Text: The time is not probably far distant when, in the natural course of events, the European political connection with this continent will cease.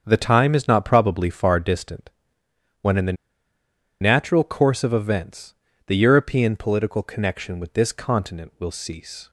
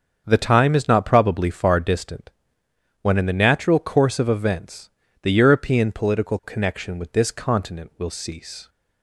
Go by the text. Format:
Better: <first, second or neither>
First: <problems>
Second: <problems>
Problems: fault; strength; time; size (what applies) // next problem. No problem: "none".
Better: second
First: starts louder than the rest; until 1.0 s; 7 dB // pauses between "distant" and "when"; noticeable; at 2.1 s; 0.72 s long // pauses between "the" and "natural"; noticeable; at 3.1 s; 0.87 s long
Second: starts louder than the rest; until 1.2 s; 7 dB // pauses between "distant" and "when"; noticeable; at 2.3 s; 0.72 s long